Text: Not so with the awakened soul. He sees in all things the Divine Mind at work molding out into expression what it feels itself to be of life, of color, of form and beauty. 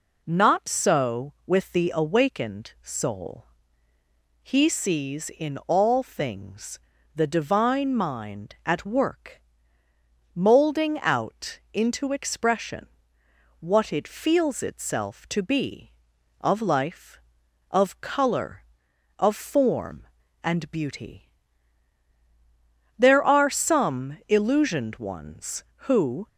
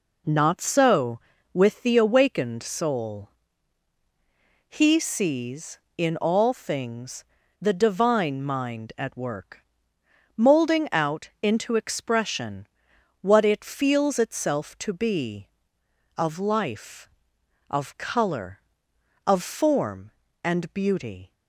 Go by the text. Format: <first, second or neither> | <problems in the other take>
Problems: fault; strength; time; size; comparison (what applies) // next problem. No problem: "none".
second | pauses between "things" and "the"; slight; at 6.7 s; 0.36 s long; also in the second // pauses between "work" and "molding"; noticeable; at 9.4 s; 0.94 s long; noticeable in the second // pauses between "out" and "into"; slight; at 11.5 s; 0.16 s long // pauses between "expression" and "what"; noticeable; at 12.8 s; 0.74 s long; noticeable in the second // goes on to say "There are some illusioned ones who"; strong; from 22.9 s on; 3.3 s long